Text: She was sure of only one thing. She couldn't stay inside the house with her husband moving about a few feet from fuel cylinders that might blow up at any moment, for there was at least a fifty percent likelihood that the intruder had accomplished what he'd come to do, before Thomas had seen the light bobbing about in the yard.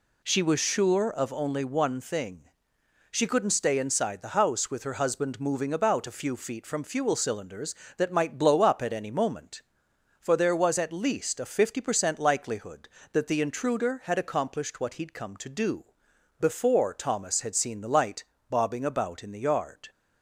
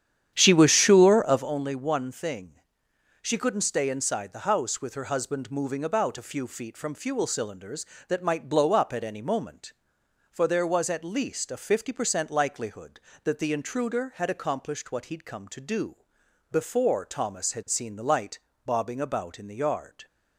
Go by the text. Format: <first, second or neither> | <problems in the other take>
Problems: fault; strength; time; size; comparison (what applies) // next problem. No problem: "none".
first | starts louder than the rest; strong; until 1.6 s; 10 dB // pauses between "light" and "bobbing"; slight; at 18.3 s; 0.26 s long; slight in the first